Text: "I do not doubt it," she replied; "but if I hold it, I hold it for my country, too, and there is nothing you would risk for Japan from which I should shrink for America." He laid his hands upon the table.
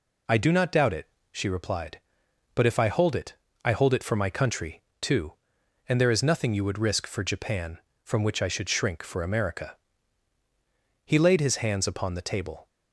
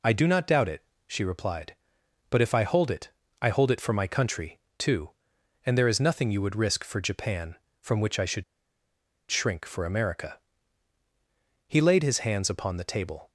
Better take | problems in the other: first | pauses between "should" and "shrink"; noticeable; at 8.4 s; 0.86 s long

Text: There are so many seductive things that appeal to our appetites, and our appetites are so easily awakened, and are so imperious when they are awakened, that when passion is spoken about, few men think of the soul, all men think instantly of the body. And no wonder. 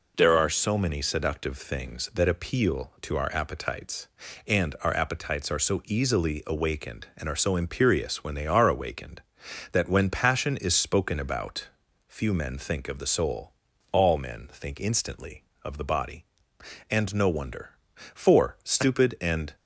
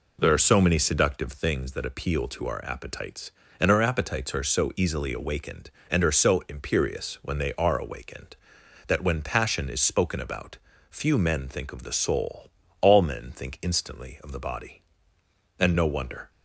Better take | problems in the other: second | goes on to say "For stupid and"; from 18.1 s on; 1.4 s long

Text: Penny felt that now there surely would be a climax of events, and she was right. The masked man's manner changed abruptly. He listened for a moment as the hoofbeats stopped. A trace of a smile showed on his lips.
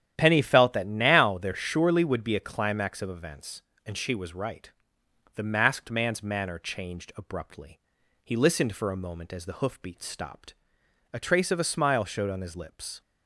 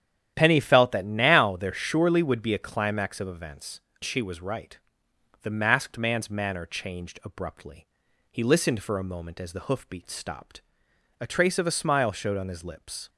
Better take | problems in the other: first | starts louder than the rest; strong; until 1.3 s; 10.5 dB; strong in the first // skips "and"; at 3.9 s

